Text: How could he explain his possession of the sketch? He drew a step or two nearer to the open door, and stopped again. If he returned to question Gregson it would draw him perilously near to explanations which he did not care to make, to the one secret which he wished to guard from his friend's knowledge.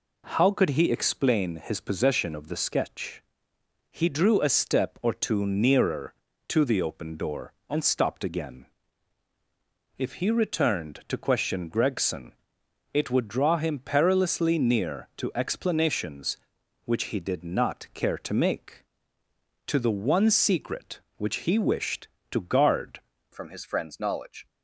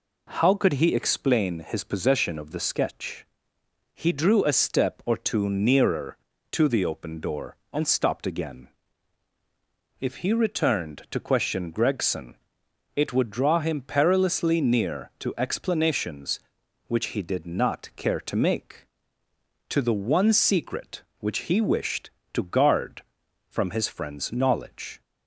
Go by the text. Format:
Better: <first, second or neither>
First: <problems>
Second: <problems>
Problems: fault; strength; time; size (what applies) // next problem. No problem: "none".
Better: second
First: pauses between "Gregson" and "it"; noticeable; at 12.3 s; 0.60 s long // changes voice at "from"; from 23.3 s on; 1.1 s long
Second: pauses between "Gregson" and "it"; noticeable; at 12.3 s; 0.60 s long